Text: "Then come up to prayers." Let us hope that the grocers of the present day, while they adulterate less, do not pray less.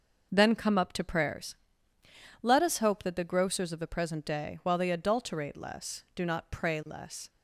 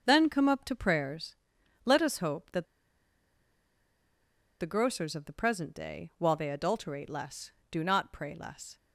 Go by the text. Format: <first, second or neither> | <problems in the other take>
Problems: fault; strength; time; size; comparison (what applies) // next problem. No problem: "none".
first | starts louder than the rest; until 1.0 s; 6.5 dB // pauses between "that" and "the"; strong; at 2.6 s; 1.9 s long